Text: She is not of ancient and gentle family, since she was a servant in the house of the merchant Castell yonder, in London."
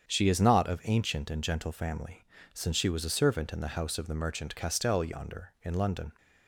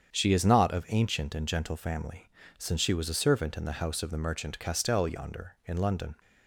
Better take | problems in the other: neither | starts louder than the rest; strong; the same in both

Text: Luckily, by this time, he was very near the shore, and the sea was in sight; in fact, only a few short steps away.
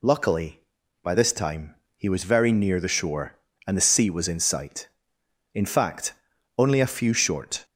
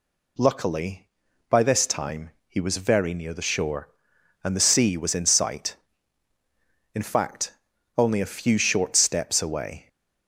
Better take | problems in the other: second | stops before "steps away"; at 7.6 s

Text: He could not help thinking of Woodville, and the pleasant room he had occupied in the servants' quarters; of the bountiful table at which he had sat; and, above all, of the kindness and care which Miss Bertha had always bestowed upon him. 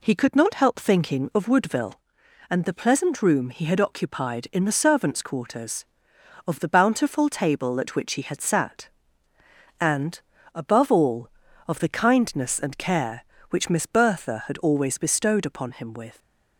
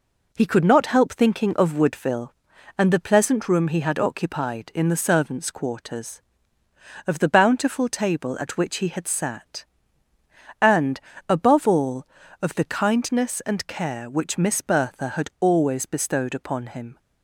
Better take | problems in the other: second | goes on to say "With"; slight; from 15.9 s on; 0.26 s long

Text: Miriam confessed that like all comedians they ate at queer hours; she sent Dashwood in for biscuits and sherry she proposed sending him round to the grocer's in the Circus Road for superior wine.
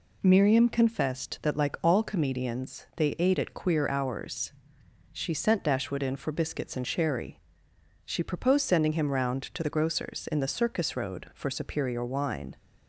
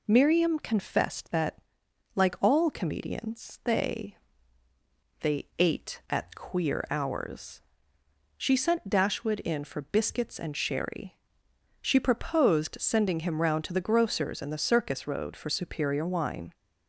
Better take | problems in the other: first | pauses between "that" and "like"; noticeable; at 1.5 s; 0.56 s long // says "they" twice; at 5.2 s // pauses between "sherry" and "she"; noticeable; at 11.1 s; 0.68 s long; noticeable in the first

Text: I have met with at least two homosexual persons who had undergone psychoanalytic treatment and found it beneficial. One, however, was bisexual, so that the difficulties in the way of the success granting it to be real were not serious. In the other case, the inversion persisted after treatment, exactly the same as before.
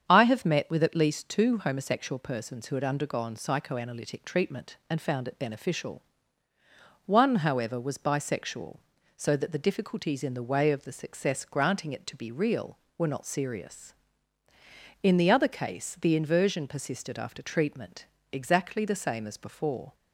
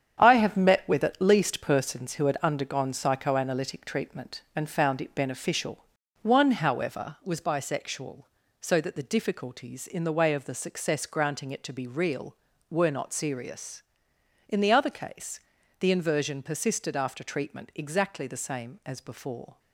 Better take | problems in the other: first | starts louder than the rest; strong; until 1.2 s; 8.5 dB; strong in the first // skips "two homosexual"; at 1.6 s

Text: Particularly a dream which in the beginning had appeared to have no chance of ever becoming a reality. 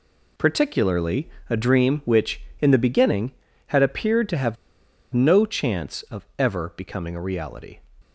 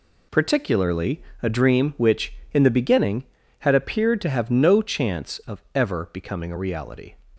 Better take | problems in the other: second | pauses between "Particularly" and "a"; slight; at 1.3 s; 0.18 s long; slight in the second // pauses between "have" and "no"; noticeable; at 4.5 s; 0.58 s long

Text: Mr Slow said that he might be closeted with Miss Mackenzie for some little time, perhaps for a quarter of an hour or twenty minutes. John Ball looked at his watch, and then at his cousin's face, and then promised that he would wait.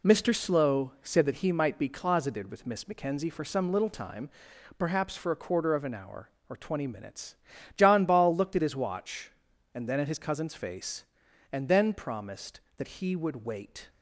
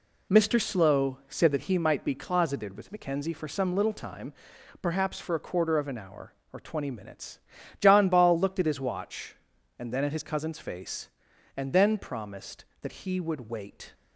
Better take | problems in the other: first | skips "Miss"; at 2.8 s

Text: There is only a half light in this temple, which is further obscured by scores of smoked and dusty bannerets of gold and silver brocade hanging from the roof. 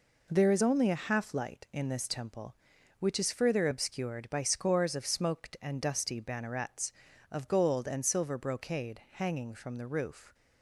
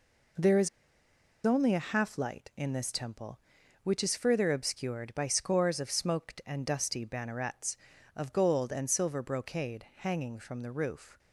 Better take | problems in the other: first | pauses between "is" and "only"; noticeable; at 0.6 s; 0.75 s long

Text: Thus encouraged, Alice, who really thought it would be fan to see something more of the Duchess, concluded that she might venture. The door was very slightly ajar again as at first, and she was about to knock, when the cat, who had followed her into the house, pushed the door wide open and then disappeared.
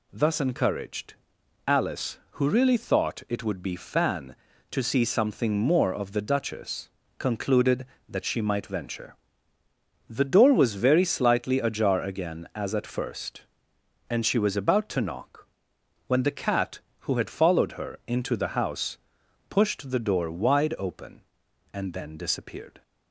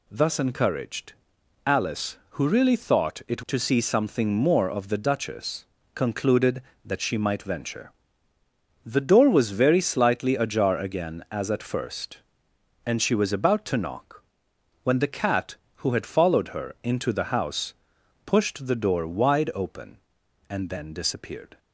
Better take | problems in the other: first | skips "would be fan"; at 3.4 s

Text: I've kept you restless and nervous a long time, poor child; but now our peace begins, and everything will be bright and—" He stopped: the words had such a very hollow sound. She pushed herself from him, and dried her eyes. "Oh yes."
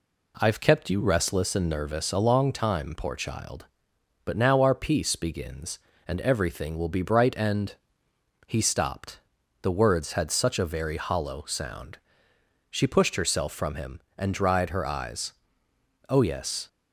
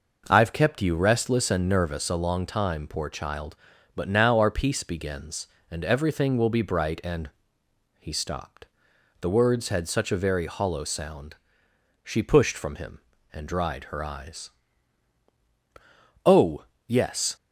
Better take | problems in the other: first | skips "herself"; at 12.5 s // pauses between "Oh" and "yes"; slight; at 16.6 s; 0.24 s long

